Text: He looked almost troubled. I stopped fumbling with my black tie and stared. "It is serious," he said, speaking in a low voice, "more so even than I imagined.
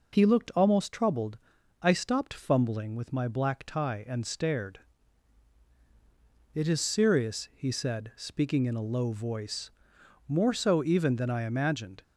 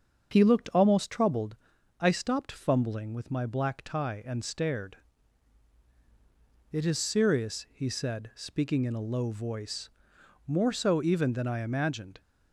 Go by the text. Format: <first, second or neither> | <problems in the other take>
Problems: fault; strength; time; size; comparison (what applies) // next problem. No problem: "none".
first | starts louder than the rest; until 1.5 s; 7 dB